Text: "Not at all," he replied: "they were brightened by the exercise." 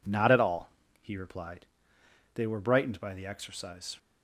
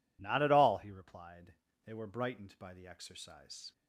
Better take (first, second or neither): neither